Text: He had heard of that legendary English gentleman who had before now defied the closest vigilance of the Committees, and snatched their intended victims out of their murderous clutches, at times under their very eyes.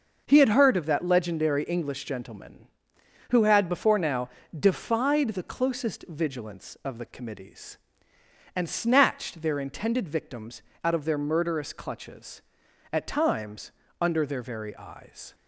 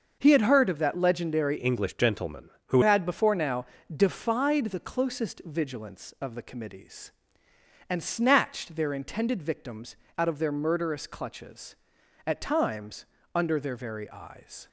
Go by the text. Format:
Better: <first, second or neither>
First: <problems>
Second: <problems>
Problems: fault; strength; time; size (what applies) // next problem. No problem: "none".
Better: first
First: starts louder than the rest; noticeable; until 1.3 s; 6 dB // pauses between "now" and "defied"; slight; at 4.2 s; 0.30 s long // pauses between "victims" and "out"; slight; at 10.6 s; 0.20 s long // pauses between "times" and "under"; slight; at 13.7 s; 0.30 s long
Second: starts louder than the rest; until 1.2 s; 6.5 dB // changes voice from "English" to "who"; from 1.5 to 2.7 s; 1.2 s long // pauses between "now" and "defied"; slight; at 3.6 s; 0.30 s long // pauses between "victims" and "out"; slight; at 9.9 s; 0.20 s long // pauses between "times" and "under"; slight; at 13.0 s; 0.30 s long